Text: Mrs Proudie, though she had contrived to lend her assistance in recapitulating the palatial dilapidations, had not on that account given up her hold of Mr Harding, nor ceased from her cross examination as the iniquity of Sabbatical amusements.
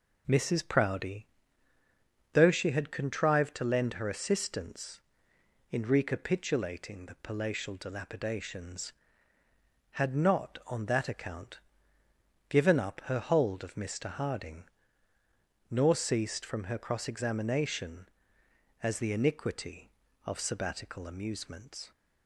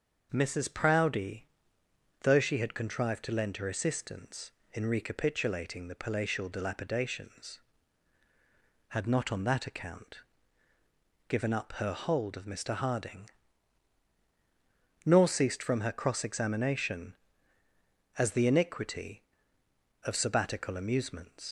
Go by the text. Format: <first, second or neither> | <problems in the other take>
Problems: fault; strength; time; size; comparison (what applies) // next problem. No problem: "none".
first | starts louder than the rest; until 1.3 s; 6.5 dB // pauses between "account" and "given"; at 10.1 s; 1.1 s long; noticeable in the first // leaves "amusements" unfinished; at 21.4 s; 90 ms